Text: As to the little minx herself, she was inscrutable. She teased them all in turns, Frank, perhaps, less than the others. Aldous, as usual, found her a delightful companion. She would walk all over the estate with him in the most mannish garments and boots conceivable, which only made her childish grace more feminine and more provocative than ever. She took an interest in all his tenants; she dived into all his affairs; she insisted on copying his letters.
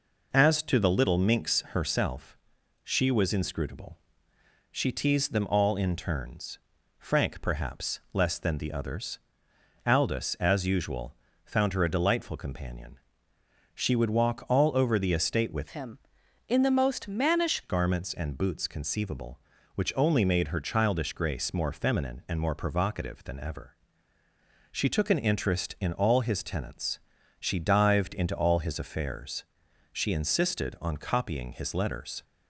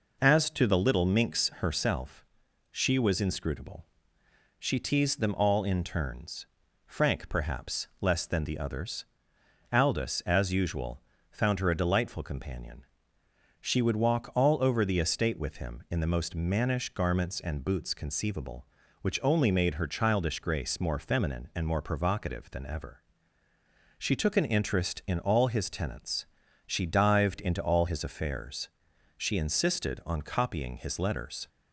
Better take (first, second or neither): second